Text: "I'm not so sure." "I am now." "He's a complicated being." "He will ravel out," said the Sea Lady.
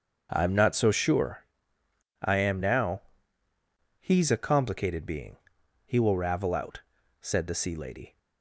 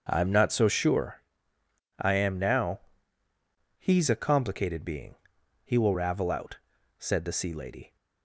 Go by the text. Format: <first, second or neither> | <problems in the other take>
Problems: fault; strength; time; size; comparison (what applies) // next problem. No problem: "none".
neither | starts louder than the rest; the same in both